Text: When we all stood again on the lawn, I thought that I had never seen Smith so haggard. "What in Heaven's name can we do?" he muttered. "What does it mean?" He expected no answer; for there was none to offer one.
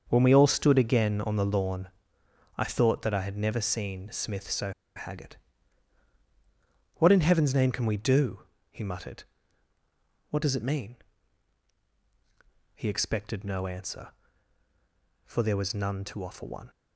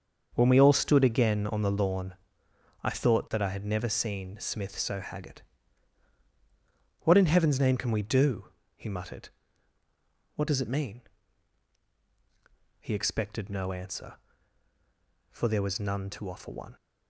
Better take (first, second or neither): second